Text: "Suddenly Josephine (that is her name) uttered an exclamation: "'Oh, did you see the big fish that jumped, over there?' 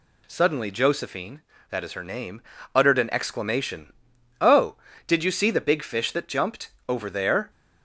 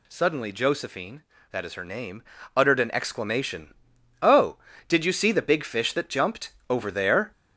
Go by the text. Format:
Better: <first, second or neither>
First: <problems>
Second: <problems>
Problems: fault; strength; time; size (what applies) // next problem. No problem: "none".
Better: first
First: none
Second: gets louder; throughout; 6.5 dB